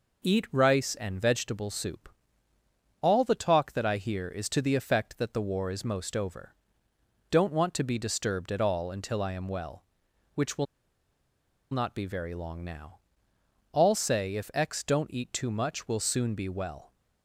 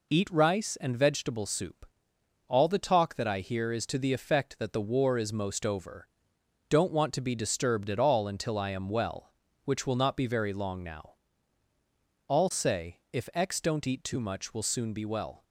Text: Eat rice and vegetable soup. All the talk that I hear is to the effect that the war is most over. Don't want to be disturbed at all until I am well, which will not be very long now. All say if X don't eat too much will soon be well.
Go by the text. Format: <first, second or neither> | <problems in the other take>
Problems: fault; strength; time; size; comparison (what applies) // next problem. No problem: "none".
second | pauses between "will" and "not"; at 10.6 s; 1.0 s long